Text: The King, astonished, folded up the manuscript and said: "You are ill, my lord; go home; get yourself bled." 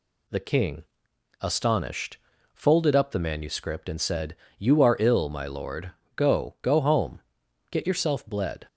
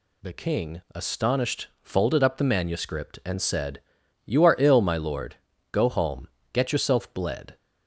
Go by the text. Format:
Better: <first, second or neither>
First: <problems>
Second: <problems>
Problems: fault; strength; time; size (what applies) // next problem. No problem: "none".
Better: second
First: says "go" twice; at 6.6 s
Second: none